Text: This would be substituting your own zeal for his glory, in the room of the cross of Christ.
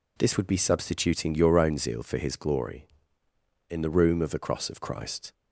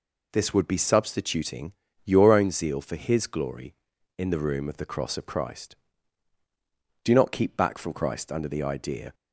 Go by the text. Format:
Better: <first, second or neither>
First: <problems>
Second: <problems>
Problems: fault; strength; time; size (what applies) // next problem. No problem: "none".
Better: first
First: none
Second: pauses between "substituting" and "your"; slight; at 1.7 s; 0.32 s long // goes on to say "Do not keep back from Christ under the idea"; strong; from 7.0 s on; 2.1 s long